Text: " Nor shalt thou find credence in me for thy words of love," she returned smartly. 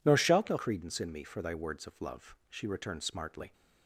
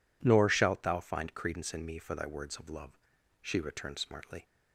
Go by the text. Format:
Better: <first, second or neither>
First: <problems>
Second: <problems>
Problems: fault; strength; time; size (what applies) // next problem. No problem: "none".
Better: second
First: skips "find"; at 0.5 s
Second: none